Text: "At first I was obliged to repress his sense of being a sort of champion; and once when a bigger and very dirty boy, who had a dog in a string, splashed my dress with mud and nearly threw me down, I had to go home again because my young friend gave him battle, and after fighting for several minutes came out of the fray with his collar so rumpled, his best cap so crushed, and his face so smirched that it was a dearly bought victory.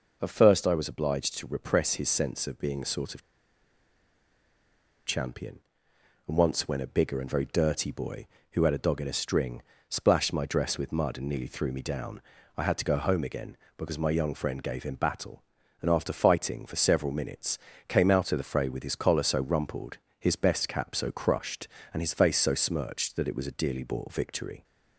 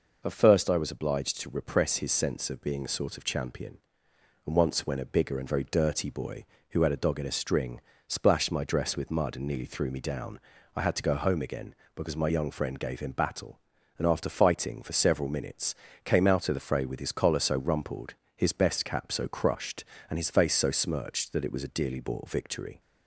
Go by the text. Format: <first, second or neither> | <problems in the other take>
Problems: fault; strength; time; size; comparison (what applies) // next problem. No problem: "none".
second | pauses between "of" and "champion"; strong; at 3.2 s; 1.8 s long // pauses between "minutes" and "came"; slight; at 17.5 s; 0.32 s long; slight in the second